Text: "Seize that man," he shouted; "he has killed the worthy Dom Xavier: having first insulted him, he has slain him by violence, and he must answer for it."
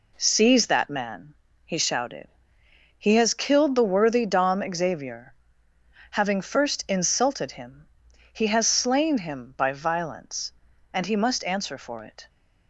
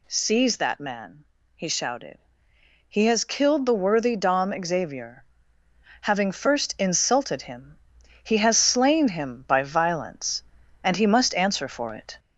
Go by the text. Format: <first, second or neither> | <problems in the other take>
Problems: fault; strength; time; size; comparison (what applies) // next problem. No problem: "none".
first | gets louder; slight; throughout; 2.5 dB